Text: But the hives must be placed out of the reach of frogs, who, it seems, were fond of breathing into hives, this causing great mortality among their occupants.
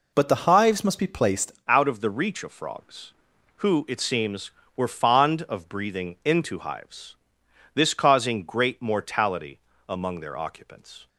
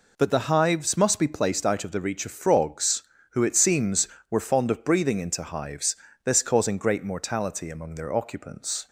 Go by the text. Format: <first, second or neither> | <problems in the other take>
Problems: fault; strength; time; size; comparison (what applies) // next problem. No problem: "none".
second | changes voice at "out"; from 1.6 s on; 9.4 s long // pauses between "mortality" and "among"; slight; at 9.5 s; 0.30 s long